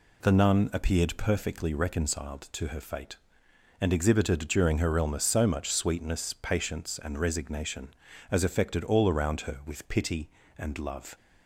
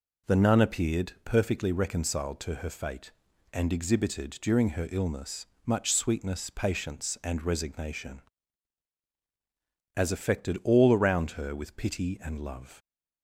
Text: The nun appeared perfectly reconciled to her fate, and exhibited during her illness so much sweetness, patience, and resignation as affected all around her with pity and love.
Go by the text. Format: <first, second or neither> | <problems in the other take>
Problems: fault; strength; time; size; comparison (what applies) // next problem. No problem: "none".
first | skips "so"; at 5.5 s